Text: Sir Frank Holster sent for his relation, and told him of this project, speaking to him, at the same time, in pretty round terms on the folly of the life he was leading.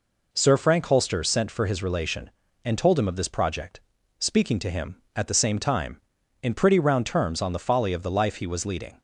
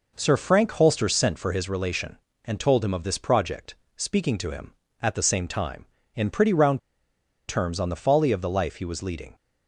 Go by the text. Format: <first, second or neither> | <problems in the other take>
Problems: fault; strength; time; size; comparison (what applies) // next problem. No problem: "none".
first | pauses between "round" and "terms"; noticeable; at 6.7 s; 0.68 s long